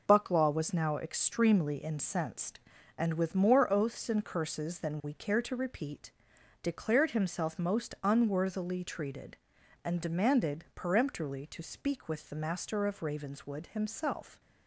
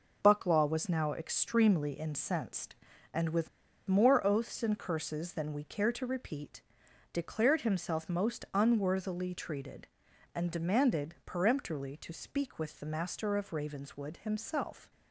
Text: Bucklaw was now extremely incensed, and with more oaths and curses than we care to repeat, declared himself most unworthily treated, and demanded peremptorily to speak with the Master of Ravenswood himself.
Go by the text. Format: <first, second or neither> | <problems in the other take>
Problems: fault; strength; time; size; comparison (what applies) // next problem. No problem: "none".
first | pauses between "with" and "more"; at 3.4 s; 0.39 s long